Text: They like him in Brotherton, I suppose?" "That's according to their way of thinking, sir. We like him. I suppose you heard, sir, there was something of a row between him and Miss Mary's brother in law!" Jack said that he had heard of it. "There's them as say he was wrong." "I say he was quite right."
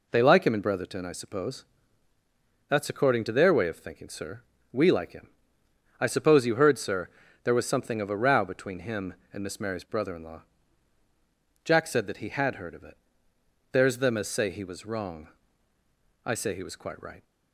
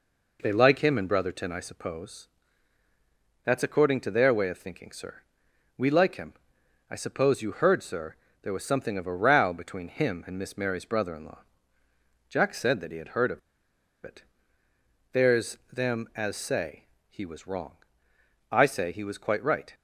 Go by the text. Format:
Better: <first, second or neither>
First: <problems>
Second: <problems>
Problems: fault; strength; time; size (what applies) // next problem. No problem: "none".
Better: first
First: none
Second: pauses between "of" and "it"; noticeable; at 13.3 s; 0.66 s long // pauses between "say" and "he"; slight; at 16.8 s; 0.24 s long